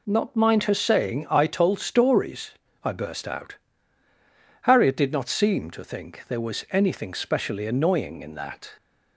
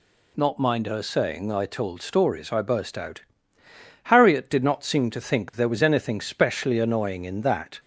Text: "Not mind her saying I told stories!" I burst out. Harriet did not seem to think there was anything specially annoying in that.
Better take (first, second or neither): neither